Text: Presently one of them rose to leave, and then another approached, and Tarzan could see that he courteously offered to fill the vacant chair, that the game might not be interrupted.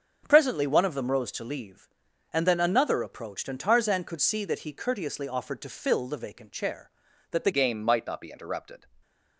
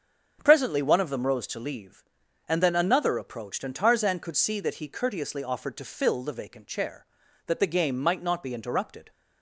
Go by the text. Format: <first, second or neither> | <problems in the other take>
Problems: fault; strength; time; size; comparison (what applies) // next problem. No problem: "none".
second | starts louder than the rest; strong; until 1.2 s; 7.5 dB; strong in the second // changes voice at "game"; from 7.5 s on; 1.3 s long // stays silent after the last word; slight; from 8.7 s on; 0.6 s long